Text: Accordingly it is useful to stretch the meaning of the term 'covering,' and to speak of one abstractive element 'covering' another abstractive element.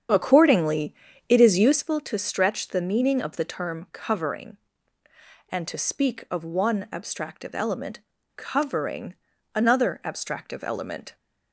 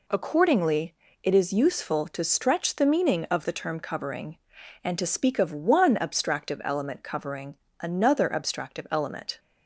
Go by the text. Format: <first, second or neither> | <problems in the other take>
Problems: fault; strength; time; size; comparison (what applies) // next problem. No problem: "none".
second | starts louder than the rest; strong; until 1.9 s; 8.5 dB // pauses between "Accordingly" and "it"; slight; at 0.9 s; 0.36 s long; slight in the second // pauses between "element" and "covering"; slight; at 8.0 s; 0.36 s long // pauses between "covering" and "another"; at 9.1 s; 0.40 s long; slight in the second